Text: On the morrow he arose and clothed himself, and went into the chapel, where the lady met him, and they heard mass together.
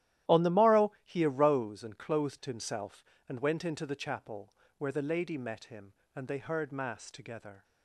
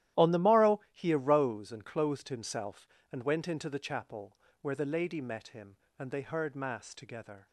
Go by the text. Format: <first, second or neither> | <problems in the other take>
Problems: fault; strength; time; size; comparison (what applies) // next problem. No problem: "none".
neither | starts louder than the rest; strong; the same in both